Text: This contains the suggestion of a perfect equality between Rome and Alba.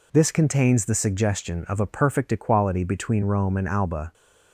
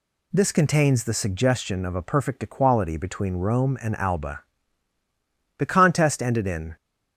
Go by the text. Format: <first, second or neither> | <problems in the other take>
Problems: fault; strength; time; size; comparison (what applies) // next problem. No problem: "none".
first | goes on to say "The contest ended in"; noticeable; from 5.5 s on; 1.1 s long